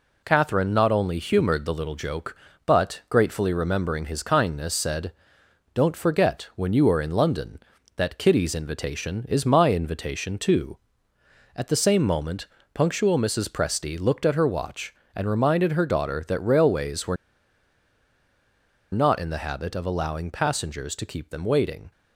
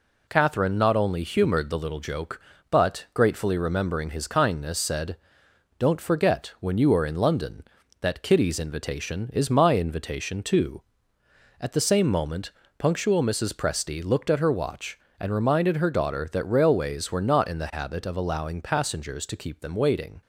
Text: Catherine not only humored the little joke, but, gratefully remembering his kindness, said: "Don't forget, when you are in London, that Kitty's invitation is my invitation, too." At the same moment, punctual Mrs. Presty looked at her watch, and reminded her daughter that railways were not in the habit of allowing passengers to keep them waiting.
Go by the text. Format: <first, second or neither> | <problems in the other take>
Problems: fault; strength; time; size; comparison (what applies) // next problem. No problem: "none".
second | pauses between "were" and "not"; strong; at 17.1 s; 1.7 s long